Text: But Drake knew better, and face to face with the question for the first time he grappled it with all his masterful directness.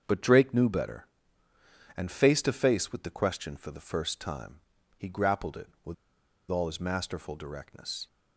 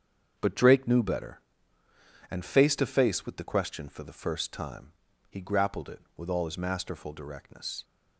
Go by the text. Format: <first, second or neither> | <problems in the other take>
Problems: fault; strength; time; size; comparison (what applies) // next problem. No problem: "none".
second | starts louder than the rest; until 1.0 s; 7 dB; also in the second // pauses between "time" and "he"; at 4.5 s; 0.38 s long; also in the second // pauses between "with" and "all"; noticeable; at 5.9 s; 0.55 s long